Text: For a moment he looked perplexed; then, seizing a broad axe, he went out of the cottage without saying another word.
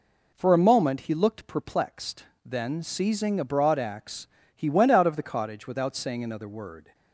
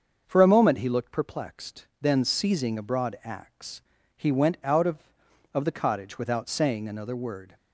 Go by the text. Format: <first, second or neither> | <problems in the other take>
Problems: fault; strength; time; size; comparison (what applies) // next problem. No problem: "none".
first | starts louder than the rest; until 1.2 s; 6.5 dB // says "of" twice; at 5.5 s